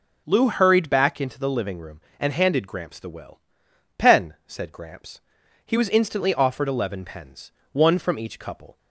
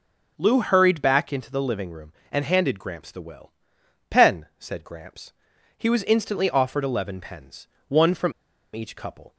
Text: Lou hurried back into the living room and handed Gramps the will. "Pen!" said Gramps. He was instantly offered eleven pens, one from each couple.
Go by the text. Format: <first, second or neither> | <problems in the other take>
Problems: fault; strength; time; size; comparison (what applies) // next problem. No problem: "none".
first | pauses between "from" and "each"; at 8.3 s; 0.42 s long